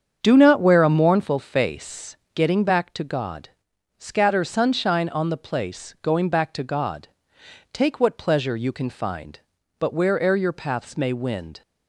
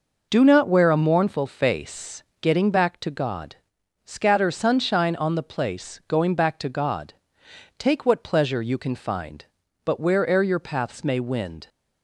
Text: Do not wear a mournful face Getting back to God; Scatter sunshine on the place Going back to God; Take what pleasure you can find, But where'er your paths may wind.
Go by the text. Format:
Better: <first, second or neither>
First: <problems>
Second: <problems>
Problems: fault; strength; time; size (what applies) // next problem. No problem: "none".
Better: second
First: starts louder than the rest; strong; until 1.5 s; 7.5 dB // pauses between "face" and "Getting"; slight; at 2.1 s; 0.18 s long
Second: pauses between "face" and "Getting"; slight; at 2.2 s; 0.18 s long